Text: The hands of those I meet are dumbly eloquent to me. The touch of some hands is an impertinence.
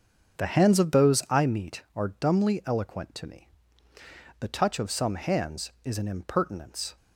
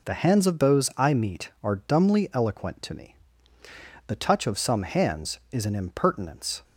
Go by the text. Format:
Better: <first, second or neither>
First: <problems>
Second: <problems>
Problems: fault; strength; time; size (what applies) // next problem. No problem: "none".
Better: second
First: starts louder than the rest; until 1.5 s; 6.5 dB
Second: none